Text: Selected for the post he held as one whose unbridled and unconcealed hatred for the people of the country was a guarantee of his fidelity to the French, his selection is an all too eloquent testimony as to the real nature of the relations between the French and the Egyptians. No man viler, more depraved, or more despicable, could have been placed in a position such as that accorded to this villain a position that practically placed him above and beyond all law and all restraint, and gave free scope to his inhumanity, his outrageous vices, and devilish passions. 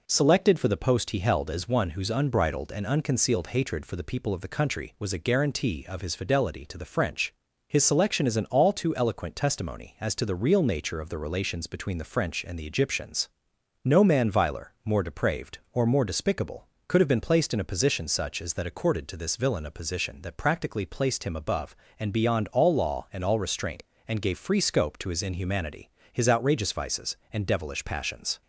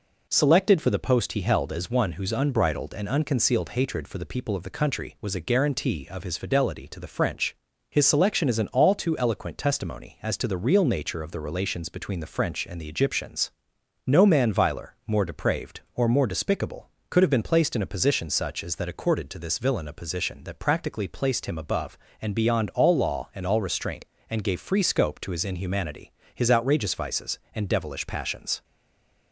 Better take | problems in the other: first | stays silent after the last word; slight; from 28.6 s on; 0.7 s long

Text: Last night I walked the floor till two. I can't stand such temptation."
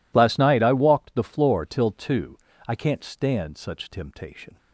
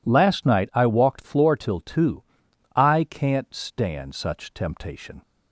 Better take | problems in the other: first | skips "the"; at 1.2 s

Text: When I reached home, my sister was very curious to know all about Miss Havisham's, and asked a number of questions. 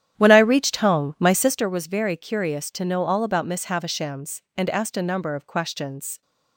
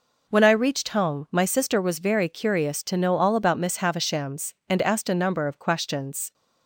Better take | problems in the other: second | starts louder than the rest; strong; until 1.6 s; 10.5 dB

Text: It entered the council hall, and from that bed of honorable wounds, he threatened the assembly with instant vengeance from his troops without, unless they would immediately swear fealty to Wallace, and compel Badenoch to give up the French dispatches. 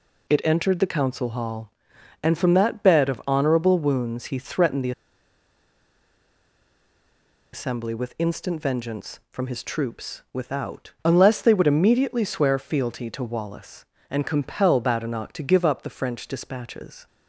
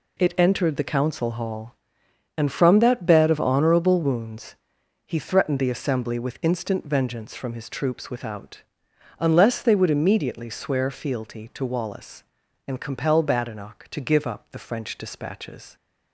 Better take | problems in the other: second | pauses between "the" and "assembly"; strong; at 4.9 s; 2.6 s long

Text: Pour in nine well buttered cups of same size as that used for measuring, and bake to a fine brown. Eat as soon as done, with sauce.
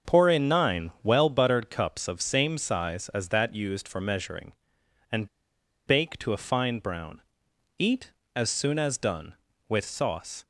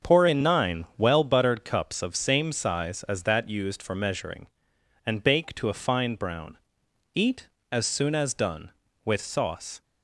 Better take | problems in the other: second | starts louder than the rest; until 1.1 s; 6.5 dB; also in the second // pauses between "and" and "bake"; noticeable; at 5.2 s; 0.58 s long

